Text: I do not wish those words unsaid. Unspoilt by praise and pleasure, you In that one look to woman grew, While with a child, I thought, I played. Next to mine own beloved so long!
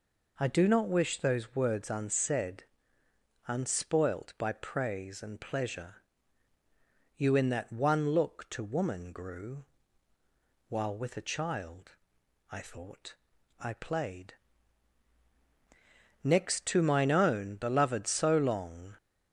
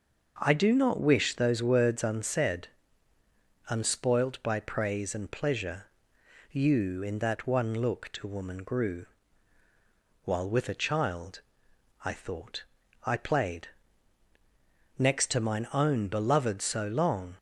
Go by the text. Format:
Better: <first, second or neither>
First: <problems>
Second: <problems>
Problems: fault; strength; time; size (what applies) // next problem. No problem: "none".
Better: neither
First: none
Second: none